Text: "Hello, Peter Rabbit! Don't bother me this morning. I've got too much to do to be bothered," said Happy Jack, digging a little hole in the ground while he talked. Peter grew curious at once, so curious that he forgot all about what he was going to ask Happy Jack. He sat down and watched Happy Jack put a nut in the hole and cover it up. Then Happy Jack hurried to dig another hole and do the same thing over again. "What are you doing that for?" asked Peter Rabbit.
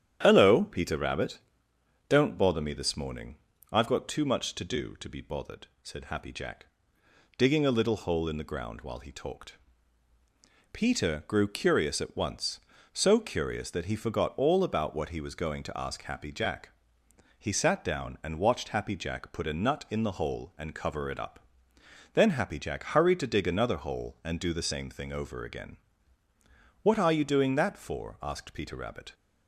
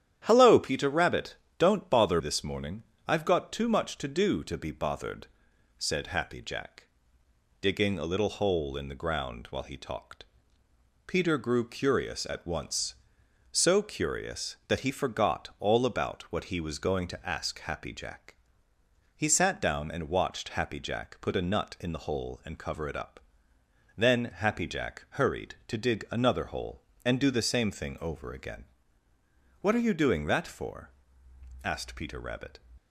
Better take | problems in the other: first | starts louder than the rest; strong; until 1.2 s; 10.5 dB; strong in the first // skips "me"; at 2.2 s

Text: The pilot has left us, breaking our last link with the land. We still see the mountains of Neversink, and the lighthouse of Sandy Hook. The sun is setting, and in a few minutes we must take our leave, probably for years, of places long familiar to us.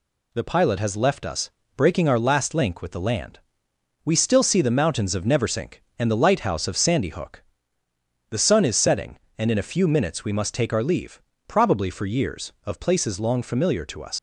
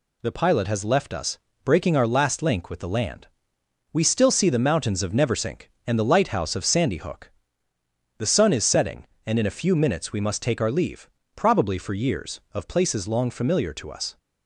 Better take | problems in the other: second | leaves "us" unfinished; at 14.1 s; 105 ms

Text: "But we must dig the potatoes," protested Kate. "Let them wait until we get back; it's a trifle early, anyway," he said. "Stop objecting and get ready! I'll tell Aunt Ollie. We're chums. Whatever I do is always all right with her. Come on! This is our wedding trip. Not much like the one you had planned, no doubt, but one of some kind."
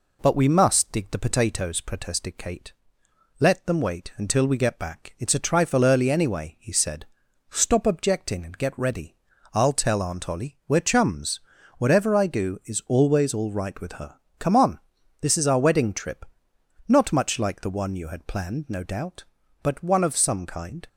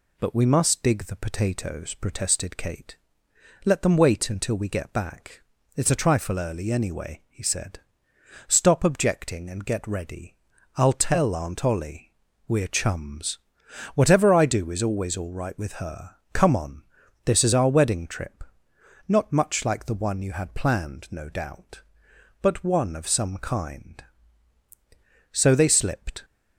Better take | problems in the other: first | goes on to say "So they slipped"; noticeable; from 25.3 s on; 0.92 s long

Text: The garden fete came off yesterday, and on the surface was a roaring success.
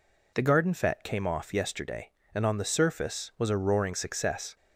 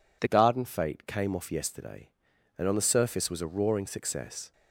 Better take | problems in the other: first | changes voice at "garden"; from 0.2 s on; 4.3 s long

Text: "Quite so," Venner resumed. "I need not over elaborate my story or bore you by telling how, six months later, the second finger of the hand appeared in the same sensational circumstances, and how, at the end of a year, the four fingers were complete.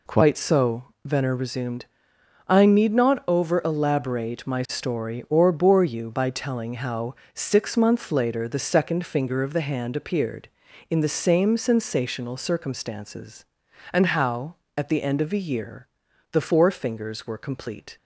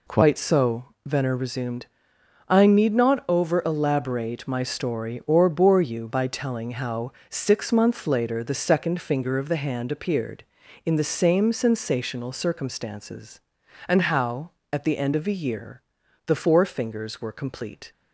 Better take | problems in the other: neither | none

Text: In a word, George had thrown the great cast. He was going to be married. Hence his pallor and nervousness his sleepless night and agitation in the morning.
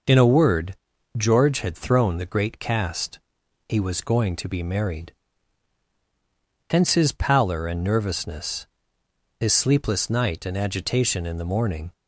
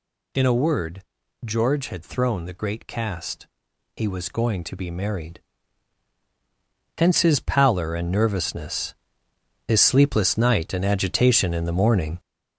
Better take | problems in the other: first | gets louder; throughout; 6.5 dB // pauses between "nervousness" and "his"; noticeable; at 8.9 s; 0.72 s long; noticeable in the first

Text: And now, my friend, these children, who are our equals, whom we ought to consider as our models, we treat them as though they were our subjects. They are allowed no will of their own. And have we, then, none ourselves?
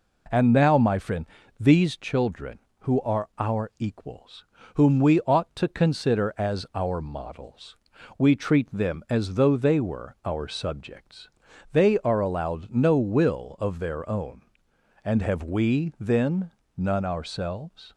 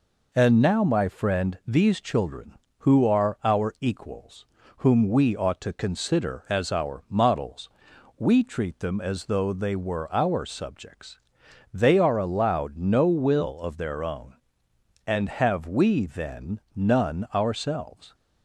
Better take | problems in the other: neither | none

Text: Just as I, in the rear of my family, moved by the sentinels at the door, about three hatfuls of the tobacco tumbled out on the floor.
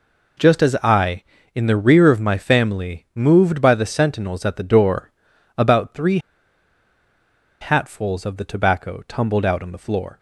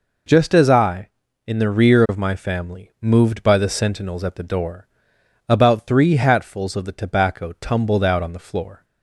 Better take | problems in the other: second | pauses between "three" and "hatfuls"; strong; at 6.2 s; 1.4 s long

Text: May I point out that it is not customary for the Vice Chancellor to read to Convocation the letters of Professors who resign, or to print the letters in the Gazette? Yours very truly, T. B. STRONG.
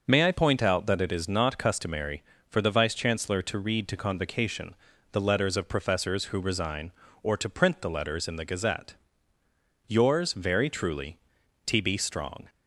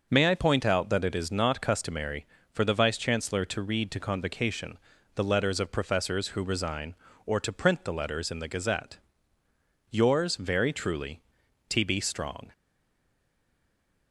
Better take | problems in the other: first | starts louder than the rest; noticeable; until 1.1 s; 6 dB; noticeable in the first // pauses between "Convocation" and "the"; at 4.7 s; 0.38 s long; also in the first // stays silent after the last word; noticeable; from 12.5 s on; 1.6 s long

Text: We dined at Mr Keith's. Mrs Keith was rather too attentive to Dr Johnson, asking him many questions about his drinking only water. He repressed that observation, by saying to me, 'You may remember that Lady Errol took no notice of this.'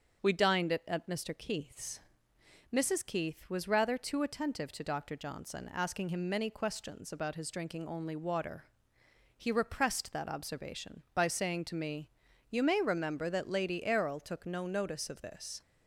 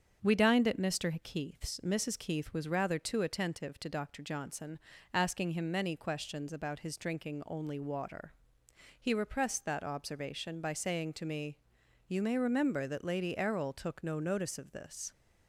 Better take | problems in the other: second | starts louder than the rest; until 1.2 s; 7 dB; also in the second // says "at" twice; at 0.8 s

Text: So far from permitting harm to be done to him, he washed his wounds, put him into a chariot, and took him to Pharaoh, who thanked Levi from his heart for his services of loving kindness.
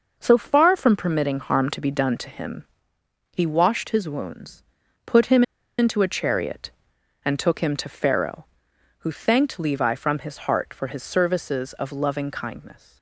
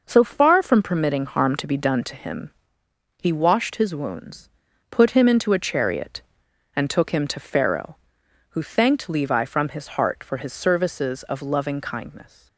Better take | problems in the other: second | pauses between "him" and "into"; slight; at 5.4 s; 0.35 s long

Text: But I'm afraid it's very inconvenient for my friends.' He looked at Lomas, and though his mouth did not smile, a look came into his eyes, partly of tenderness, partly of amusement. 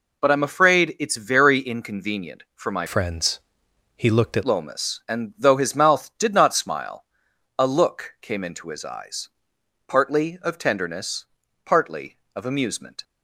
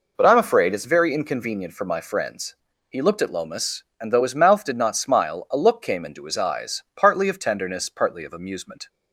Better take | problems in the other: second | changes voice from "friends" to "at"; from 2.8 to 4.4 s; 1.6 s long

